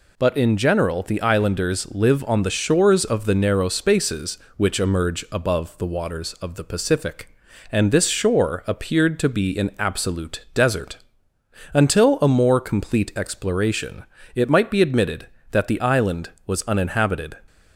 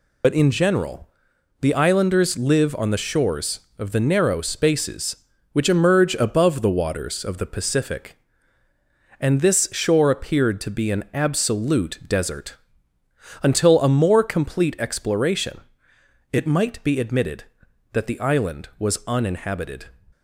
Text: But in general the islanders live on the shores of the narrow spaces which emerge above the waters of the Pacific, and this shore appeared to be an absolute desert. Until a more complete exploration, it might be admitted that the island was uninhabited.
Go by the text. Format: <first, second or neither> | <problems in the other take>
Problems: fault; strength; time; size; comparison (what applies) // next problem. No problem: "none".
first | loses the start of "But"; at 0.2 s; 60 ms // pauses between "general" and "the"; noticeable; at 1.0 s; 0.54 s long